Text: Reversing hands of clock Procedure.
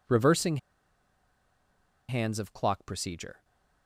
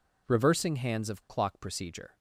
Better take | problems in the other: second | pauses between "Reversing" and "hands"; strong; at 0.5 s; 1.5 s long

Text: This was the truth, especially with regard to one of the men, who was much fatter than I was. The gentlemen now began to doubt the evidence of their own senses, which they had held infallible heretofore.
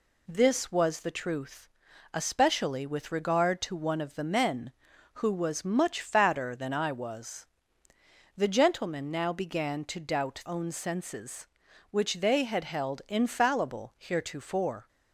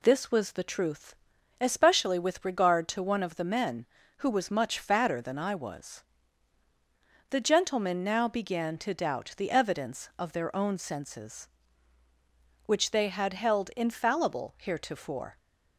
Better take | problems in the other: second | skips "the evidence of their"; at 10.4 s

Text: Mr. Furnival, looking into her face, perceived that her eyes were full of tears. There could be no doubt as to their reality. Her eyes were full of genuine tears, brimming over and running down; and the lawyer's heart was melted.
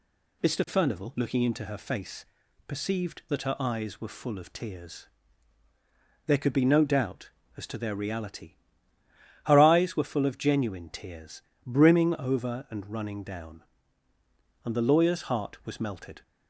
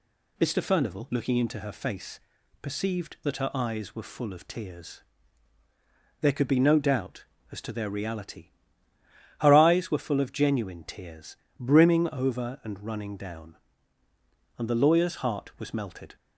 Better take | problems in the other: neither | none

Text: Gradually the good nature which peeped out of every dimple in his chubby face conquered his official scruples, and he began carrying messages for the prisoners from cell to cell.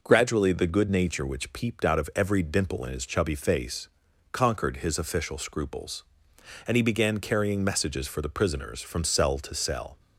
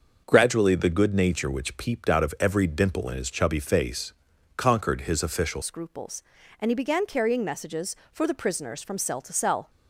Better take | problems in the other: first | starts louder than the rest; until 1.2 s; 6 dB // pauses between "face" and "conquered"; at 4.1 s; 0.42 s long; also in the first // changes voice at "scruples"; from 5.6 s on; 4.0 s long

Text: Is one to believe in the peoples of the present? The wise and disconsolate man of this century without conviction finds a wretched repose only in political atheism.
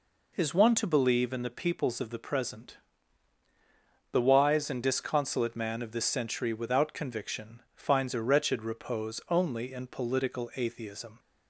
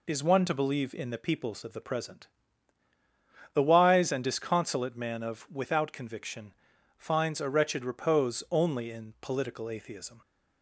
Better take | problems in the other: first | skips "this century"; at 5.4 s // pauses between "conviction" and "finds"; at 6.5 s; 0.44 s long

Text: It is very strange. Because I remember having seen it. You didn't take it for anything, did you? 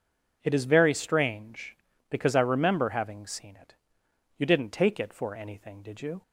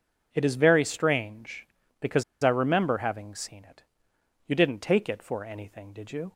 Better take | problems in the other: first | pauses between "Because" and "I"; slight; at 2.2 s; 0.18 s long

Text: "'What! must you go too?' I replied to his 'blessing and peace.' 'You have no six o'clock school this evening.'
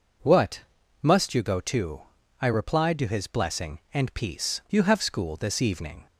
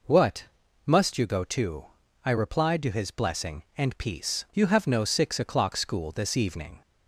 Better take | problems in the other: second | skips "no six o'clock"; at 5.0 s

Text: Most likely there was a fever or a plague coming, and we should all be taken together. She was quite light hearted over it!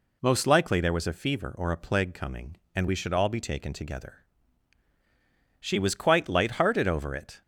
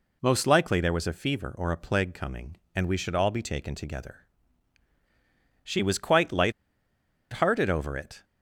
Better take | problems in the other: first | pauses between "light" and "hearted"; noticeable; at 6.5 s; 0.81 s long

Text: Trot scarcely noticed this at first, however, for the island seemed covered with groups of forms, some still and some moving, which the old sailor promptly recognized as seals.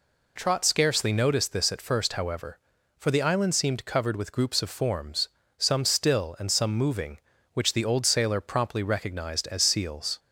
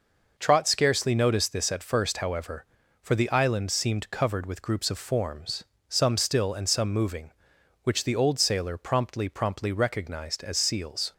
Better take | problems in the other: first | says "promptly" twice; at 9.2 s

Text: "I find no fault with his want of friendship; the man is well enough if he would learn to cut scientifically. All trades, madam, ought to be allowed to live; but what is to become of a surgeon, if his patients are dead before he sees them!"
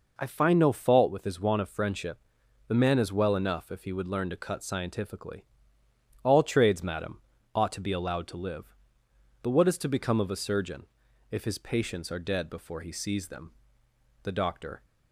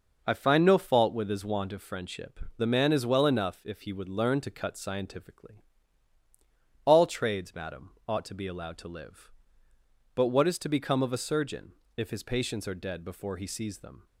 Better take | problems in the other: second | goes on to say "The doctor"; noticeable; from 14.2 s on; 0.62 s long

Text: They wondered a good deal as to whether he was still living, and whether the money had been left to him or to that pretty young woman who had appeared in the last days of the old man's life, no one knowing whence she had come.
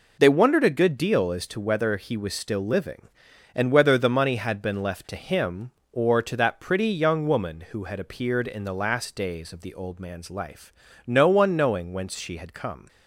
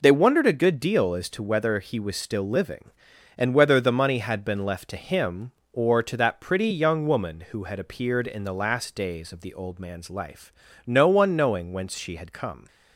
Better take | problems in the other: neither | none

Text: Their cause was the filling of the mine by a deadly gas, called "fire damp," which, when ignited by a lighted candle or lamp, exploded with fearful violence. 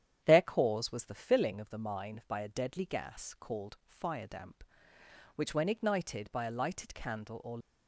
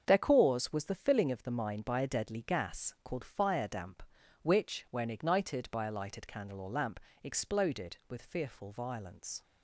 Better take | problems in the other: second | starts louder than the rest; strong; until 1.2 s; 9.5 dB; also in the second // stops before "lamp exploded with fearful violence"; at 7.6 s

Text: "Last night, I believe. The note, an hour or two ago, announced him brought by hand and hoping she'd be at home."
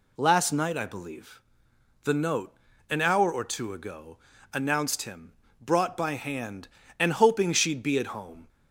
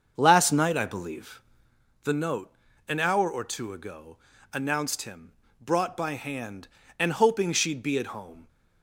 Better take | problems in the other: first | starts louder than the rest; until 1.8 s; 6.5 dB // pauses between "him" and "brought"; slight; at 5.3 s; 0.26 s long; slight in the first

